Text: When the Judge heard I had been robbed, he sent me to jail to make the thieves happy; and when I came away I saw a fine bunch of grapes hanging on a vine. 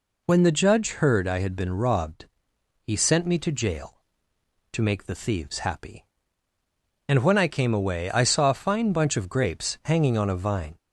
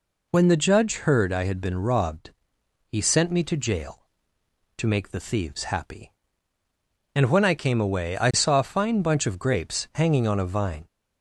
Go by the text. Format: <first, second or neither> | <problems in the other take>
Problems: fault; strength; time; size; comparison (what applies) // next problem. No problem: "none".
neither | none